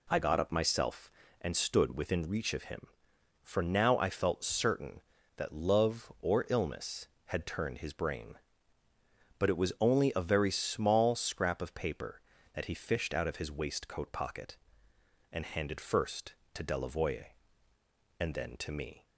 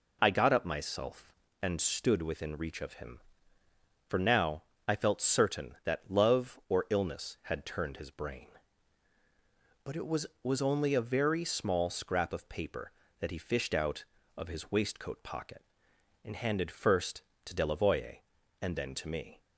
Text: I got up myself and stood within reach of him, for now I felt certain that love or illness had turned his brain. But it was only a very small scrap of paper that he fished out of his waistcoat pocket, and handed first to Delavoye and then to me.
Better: first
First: none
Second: pauses between "now" and "I"; slight; at 4.6 s; 0.22 s long // says "was" twice; at 10.4 s

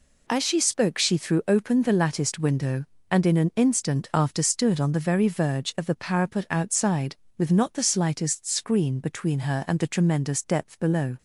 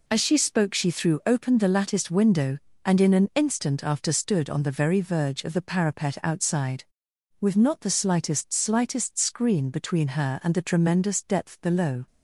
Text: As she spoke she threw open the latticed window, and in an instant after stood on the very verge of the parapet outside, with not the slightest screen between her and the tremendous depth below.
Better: first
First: none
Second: says "slightest" twice; at 8.5 s

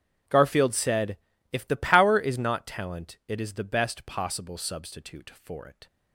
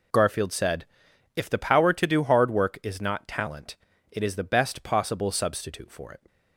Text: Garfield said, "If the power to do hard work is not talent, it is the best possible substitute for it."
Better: second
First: starts louder than the rest; strong; until 1.6 s; 9 dB // skips "to do hard work"; at 2.1 s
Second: none

